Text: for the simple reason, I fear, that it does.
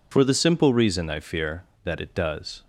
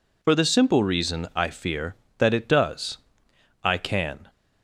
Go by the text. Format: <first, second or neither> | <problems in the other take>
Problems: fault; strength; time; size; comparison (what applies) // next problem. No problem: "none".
first | goes on to say "I can"; noticeable; from 3.6 s on; 0.66 s long